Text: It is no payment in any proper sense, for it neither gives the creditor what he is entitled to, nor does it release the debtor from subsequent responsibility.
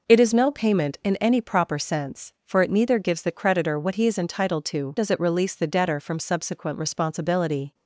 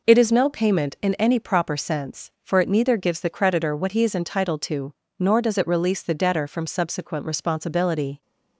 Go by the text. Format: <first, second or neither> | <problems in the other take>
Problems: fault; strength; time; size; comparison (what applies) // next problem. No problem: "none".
second | skips "nor"; at 4.9 s